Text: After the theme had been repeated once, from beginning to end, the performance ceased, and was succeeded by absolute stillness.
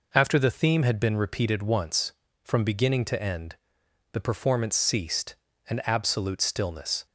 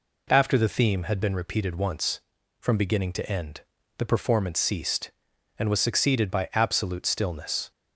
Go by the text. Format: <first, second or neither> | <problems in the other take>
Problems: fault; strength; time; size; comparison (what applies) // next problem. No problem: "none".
second | skips "was succeeded by"; at 5.8 s